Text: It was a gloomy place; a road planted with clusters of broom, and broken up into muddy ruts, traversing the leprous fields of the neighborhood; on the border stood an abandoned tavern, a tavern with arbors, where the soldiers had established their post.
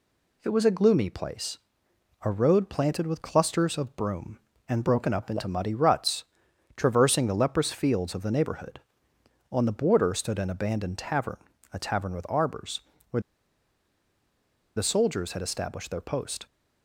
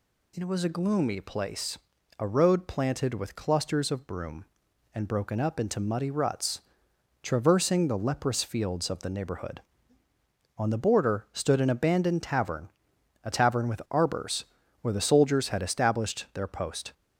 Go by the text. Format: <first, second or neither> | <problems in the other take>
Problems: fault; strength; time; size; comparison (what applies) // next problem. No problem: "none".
second | pauses between "where" and "the"; strong; at 13.1 s; 1.5 s long